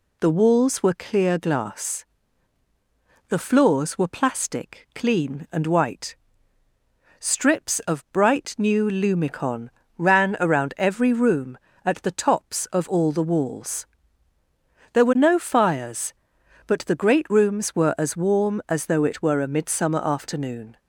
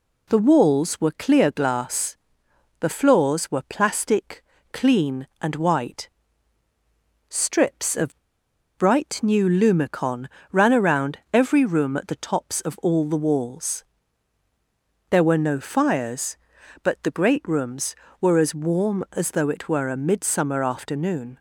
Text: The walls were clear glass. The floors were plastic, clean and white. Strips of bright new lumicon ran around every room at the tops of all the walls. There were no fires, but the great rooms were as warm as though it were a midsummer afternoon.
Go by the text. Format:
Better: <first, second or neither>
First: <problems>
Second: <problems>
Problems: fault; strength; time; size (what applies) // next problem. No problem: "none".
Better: first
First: pauses between "lumicon" and "ran"; slight; at 9.6 s; 0.30 s long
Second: pauses between "of" and "bright"; noticeable; at 8.1 s; 0.60 s long // pauses between "lumicon" and "ran"; slight; at 10.2 s; 0.24 s long